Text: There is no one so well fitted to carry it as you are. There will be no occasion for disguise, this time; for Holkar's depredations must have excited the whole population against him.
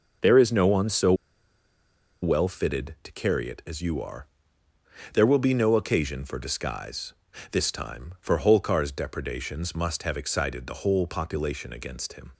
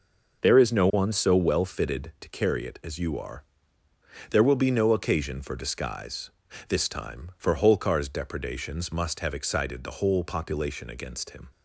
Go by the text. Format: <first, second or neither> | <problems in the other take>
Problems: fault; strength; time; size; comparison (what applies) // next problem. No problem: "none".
second | pauses between "so" and "well"; at 1.1 s; 1.0 s long